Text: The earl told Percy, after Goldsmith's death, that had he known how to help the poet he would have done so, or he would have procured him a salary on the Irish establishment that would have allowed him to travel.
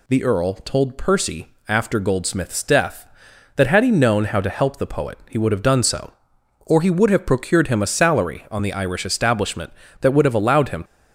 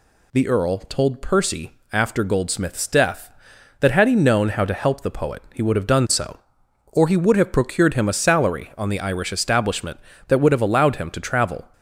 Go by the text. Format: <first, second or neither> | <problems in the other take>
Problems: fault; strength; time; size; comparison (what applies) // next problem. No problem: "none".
second | stops before "to travel"; at 10.8 s